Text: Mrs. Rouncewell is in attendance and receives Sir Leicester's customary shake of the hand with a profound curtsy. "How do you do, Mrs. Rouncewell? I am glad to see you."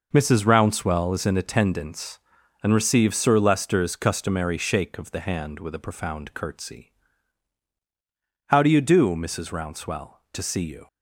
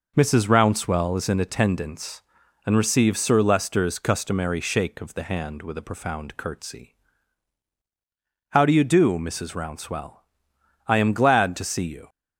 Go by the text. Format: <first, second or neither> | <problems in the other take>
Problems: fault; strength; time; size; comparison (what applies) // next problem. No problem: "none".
second | skips "I am glad"; at 10.2 s